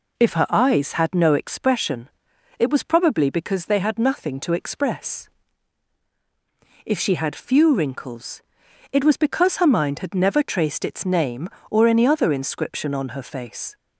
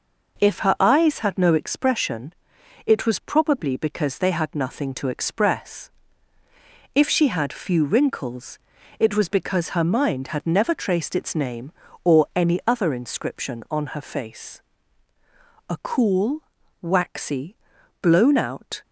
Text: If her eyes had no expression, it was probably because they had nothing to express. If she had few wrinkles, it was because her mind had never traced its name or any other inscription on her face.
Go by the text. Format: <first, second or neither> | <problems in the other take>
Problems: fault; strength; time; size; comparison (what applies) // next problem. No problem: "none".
first | goes on to say "A cool waxy blown out"; strong; from 15.6 s on; 3.1 s long